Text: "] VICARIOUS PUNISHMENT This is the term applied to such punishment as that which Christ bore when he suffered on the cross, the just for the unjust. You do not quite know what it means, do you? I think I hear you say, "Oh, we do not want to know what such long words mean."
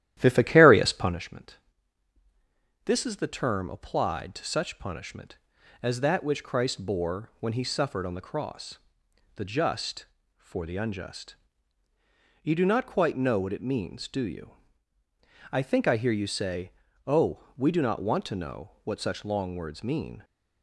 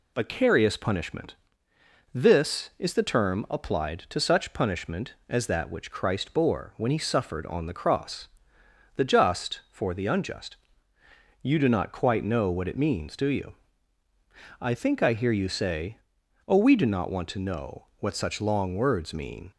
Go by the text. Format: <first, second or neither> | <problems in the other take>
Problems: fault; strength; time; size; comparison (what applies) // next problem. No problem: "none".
second | starts louder than the rest; strong; until 1.2 s; 12.5 dB // pauses between "PUNISHMENT" and "This"; strong; at 1.5 s; 1.2 s long; noticeable in the second